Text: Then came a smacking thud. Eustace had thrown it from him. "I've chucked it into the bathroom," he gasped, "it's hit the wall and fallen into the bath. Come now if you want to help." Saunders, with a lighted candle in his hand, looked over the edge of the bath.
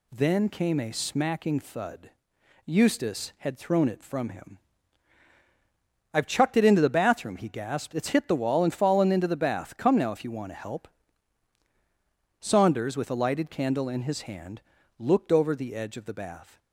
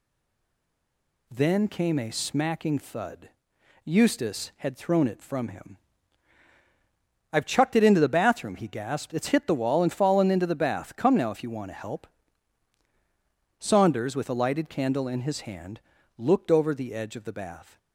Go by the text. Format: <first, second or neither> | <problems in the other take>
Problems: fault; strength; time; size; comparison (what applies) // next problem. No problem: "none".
first | stays silent before the first word; noticeable; until 1.2 s; 1.2 s long